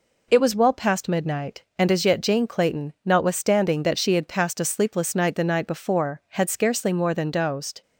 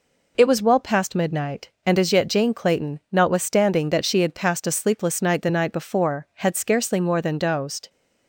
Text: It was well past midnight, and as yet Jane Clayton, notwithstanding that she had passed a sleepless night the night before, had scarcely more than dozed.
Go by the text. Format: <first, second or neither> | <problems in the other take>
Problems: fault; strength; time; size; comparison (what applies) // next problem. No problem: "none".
neither | none